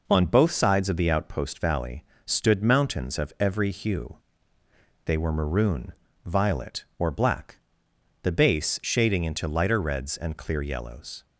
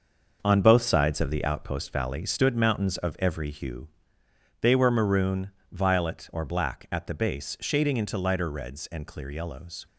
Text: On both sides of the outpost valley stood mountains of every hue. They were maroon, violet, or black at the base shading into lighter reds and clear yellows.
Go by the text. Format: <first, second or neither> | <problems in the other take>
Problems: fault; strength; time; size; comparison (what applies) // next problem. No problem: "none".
second | pauses between "valley" and "stood"; slight; at 2.0 s; 0.24 s long // skips "at"; at 7.8 s